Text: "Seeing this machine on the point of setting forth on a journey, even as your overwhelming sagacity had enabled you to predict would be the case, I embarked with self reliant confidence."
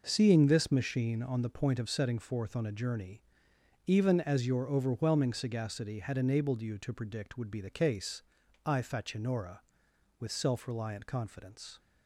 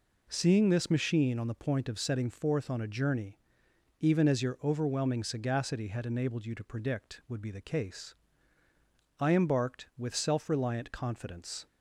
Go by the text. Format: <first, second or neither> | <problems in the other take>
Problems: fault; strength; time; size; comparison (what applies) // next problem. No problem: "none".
second | says "facinora" for "embarked"; at 8.8 s